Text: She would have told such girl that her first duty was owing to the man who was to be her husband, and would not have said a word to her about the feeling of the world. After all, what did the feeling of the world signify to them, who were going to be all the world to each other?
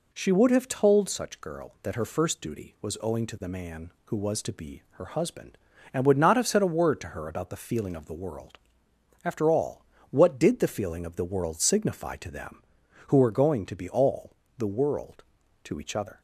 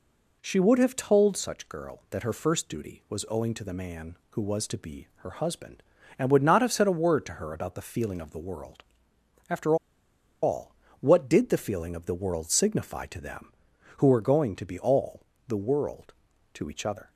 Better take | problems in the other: first | pauses between "After" and "all"; noticeable; at 9.7 s; 0.67 s long // pauses between "all" and "the"; slight; at 15.2 s; 0.26 s long; slight in the first

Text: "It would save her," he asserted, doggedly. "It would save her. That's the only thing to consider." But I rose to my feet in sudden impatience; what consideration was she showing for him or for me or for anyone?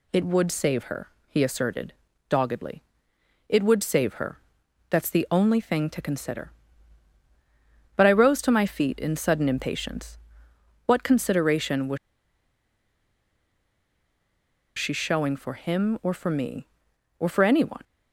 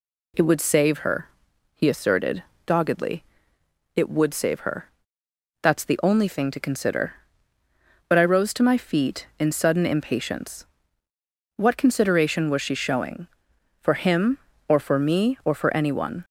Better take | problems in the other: second | pauses between "was" and "she"; strong; at 11.9 s; 2.8 s long

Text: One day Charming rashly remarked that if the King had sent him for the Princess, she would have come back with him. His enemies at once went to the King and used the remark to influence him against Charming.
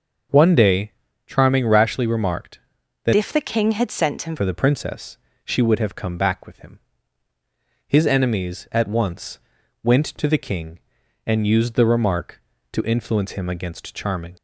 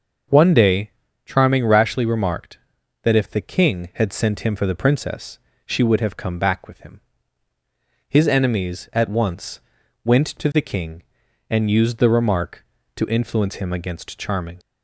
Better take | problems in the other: second | starts louder than the rest; until 1.6 s; 6.5 dB; also in the second // pauses between "day" and "Charming"; slight; at 0.9 s; 0.34 s long; slight in the second // changes voice from "if" to "him"; from 3.1 to 4.3 s; 1.2 s long // pauses between "once" and "went"; noticeable; at 9.3 s; 0.46 s long; noticeable in the second

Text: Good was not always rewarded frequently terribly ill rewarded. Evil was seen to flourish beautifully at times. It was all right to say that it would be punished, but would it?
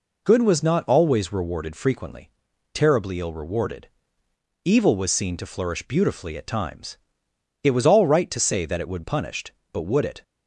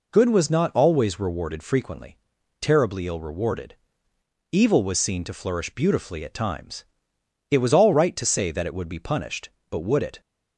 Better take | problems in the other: second | pauses between "frequently" and "terribly"; at 2.2 s; 0.44 s long; also in the second // skips "be"; at 9.0 s

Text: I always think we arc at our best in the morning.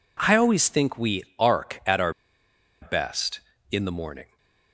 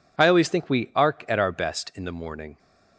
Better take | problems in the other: second | pauses between "we" and "arc"; slight; at 1.2 s; 0.16 s long // pauses between "our" and "best"; noticeable; at 2.1 s; 0.69 s long

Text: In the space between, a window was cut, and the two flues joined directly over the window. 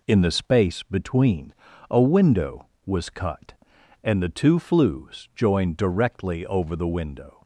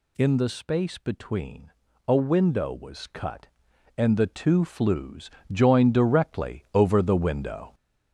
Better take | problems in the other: first | gets louder; throughout; 6.5 dB // pauses between "flues" and "joined"; slight; at 5.2 s; 0.24 s long

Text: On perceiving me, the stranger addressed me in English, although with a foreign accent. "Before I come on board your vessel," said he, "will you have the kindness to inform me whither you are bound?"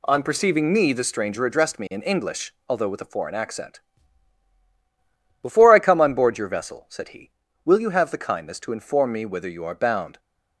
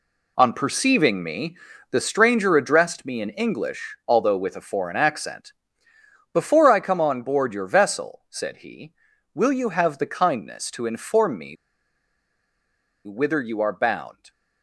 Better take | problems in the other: first | pauses between "me" and "whither"; strong; at 11.5 s; 1.5 s long

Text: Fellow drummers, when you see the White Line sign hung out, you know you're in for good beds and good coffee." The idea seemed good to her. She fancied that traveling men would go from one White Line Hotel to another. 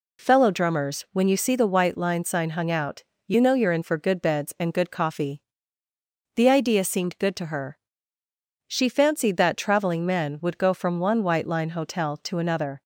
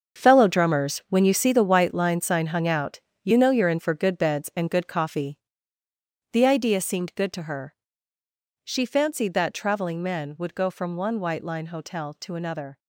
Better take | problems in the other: first | gets quieter; strong; throughout; 12 dB

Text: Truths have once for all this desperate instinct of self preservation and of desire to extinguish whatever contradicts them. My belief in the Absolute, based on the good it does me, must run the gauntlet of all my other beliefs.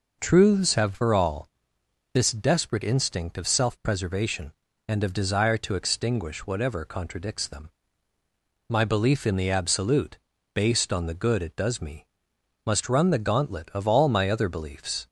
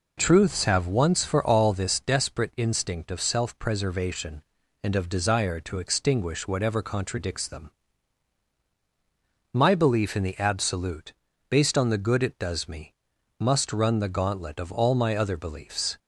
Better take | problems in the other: second | skips "once"; at 0.9 s // pauses between "all" and "this"; noticeable; at 1.4 s; 0.64 s long

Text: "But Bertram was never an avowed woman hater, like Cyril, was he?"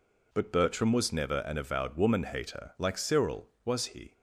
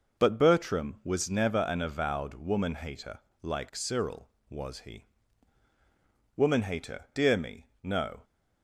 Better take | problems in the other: first | goes on to say "Woman hater dear me no"; strong; from 6.3 s on; 1.8 s long

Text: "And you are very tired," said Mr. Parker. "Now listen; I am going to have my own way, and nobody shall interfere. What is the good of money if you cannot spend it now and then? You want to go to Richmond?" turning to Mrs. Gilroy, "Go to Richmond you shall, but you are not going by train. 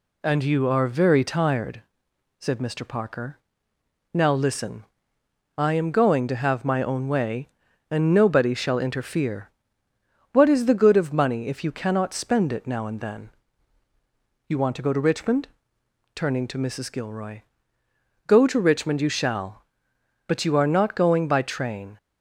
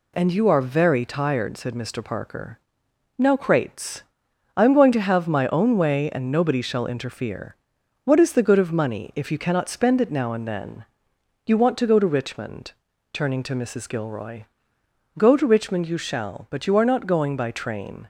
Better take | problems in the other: first | says "crates" for "listen"; at 3.3 s

